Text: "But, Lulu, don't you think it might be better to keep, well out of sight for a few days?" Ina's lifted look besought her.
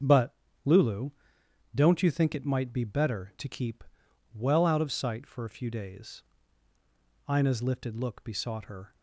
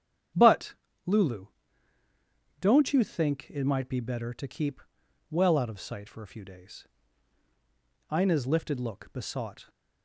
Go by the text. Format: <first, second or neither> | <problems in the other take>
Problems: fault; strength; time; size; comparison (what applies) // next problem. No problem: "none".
first | starts louder than the rest; strong; until 2.7 s; 9 dB; strong in the first // stops before "her"; at 9.6 s